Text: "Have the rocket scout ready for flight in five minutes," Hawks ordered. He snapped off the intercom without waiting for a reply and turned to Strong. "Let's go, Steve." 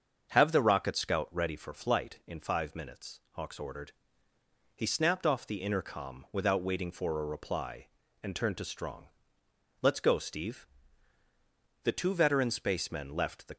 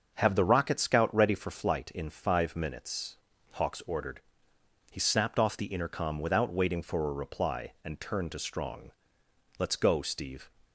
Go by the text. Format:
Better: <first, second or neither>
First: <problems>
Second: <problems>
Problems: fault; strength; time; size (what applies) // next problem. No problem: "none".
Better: second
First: starts louder than the rest; until 1.3 s; 6.5 dB // goes on to say "The two veteran spacemen left the"; strong; from 11.8 s on; 1.7 s long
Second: starts louder than the rest; until 1.1 s; 6.5 dB